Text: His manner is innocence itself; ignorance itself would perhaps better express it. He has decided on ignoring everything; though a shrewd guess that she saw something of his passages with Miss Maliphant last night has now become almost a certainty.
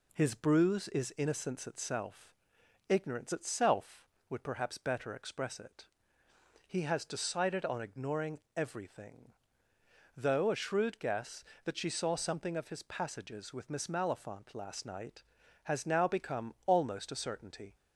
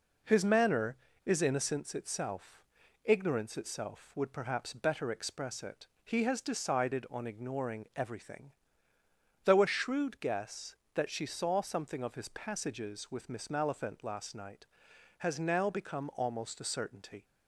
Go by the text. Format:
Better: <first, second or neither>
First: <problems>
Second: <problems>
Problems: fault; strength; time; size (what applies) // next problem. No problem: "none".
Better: second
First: says "bruise" for "manner"; at 0.3 s // pauses between "ignoring" and "everything"; slight; at 8.4 s; 0.16 s long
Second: none